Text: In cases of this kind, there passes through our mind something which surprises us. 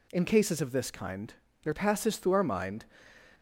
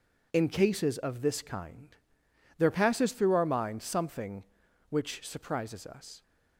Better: second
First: stops before "something which surprises us"; at 3.3 s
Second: none

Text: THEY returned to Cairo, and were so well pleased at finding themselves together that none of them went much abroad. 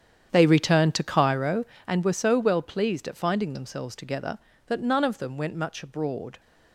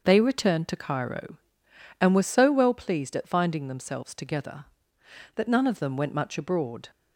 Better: second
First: starts louder than the rest; strong; until 1.9 s; 9 dB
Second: none

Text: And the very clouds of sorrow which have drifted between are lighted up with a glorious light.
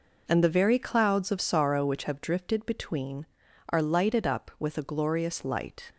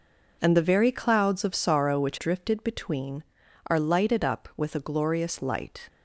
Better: first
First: none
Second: skips "have"; at 2.1 s

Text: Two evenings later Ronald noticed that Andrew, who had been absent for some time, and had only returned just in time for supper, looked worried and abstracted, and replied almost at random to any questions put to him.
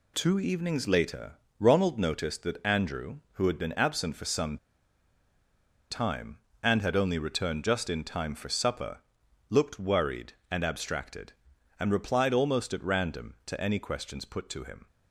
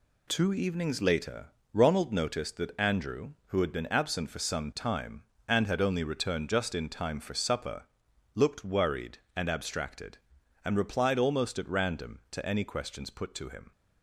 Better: second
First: pauses between "later" and "Ronald"; slight; at 1.3 s; 0.26 s long // pauses between "some" and "time"; strong; at 4.5 s; 1.3 s long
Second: pauses between "later" and "Ronald"; slight; at 1.4 s; 0.26 s long

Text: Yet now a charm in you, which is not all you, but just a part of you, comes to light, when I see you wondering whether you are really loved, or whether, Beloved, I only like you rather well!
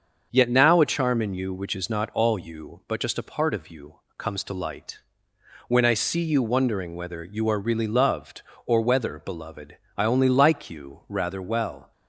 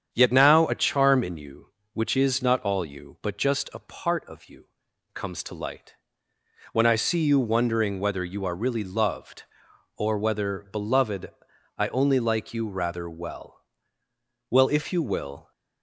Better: first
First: starts louder than the rest; until 1.3 s; 6.5 dB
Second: starts louder than the rest; strong; until 1.1 s; 8 dB // goes on to say "Well if you will"; noticeable; from 14.5 s on; 1.0 s long

